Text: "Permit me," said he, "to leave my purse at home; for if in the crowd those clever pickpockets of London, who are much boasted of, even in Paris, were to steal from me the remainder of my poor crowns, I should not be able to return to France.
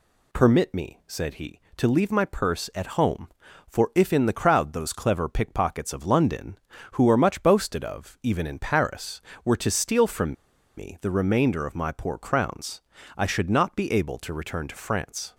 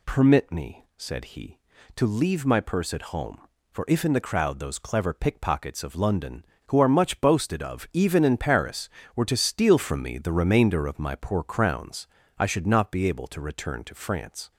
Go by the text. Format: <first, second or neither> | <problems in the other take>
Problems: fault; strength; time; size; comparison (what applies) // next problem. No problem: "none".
second | pauses between "from" and "me"; at 10.3 s; 0.43 s long